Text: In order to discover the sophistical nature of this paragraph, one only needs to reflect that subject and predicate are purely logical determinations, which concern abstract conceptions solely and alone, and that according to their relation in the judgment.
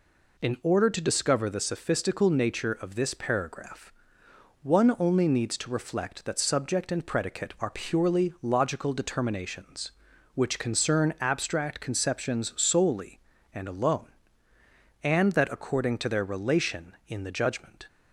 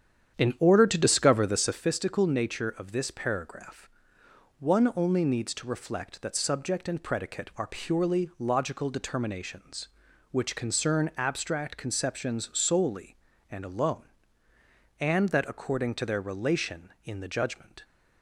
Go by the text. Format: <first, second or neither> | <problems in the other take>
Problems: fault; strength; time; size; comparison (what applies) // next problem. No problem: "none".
first | starts louder than the rest; strong; until 1.9 s; 9 dB